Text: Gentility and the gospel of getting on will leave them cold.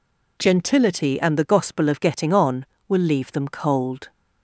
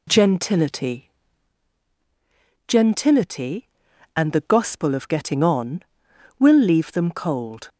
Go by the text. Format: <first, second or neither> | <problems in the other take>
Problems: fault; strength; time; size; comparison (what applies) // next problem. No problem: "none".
first | says "Gentility" twice; at 2.6 s